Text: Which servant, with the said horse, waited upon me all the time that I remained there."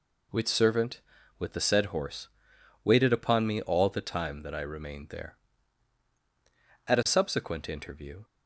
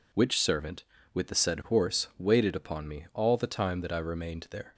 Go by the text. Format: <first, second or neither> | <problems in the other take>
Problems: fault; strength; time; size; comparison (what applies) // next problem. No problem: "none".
second | goes on to say "At a subsequent interview"; from 6.8 s on; 1.3 s long